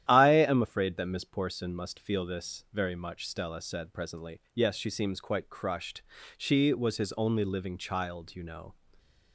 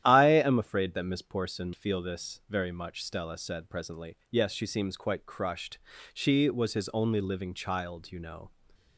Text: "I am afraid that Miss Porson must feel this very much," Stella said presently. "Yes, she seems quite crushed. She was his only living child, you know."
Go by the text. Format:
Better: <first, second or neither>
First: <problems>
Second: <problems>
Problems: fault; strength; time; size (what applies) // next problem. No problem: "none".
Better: first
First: starts louder than the rest; strong; until 1.1 s; 11.5 dB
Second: starts louder than the rest; strong; until 1.0 s; 11.5 dB // skips "must"; at 1.7 s